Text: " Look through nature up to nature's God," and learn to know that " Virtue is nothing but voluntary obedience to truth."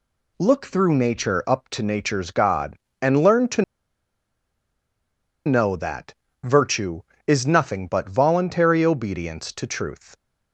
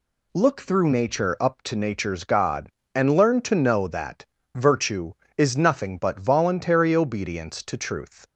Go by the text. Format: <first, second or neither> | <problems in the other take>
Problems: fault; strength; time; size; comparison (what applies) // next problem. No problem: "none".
second | pauses between "to" and "know"; strong; at 3.6 s; 1.8 s long